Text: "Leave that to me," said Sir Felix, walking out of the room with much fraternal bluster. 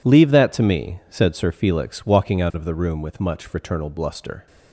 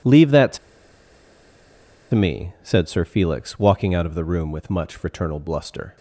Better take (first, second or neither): first